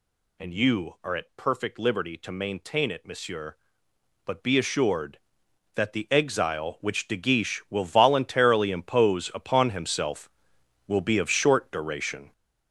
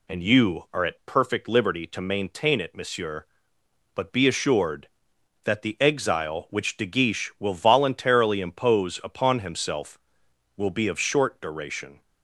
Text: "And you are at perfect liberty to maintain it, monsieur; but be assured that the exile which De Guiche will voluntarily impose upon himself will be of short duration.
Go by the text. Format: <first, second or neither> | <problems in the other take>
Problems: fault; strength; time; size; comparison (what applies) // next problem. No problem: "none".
second | gets louder; strong; throughout; 8 dB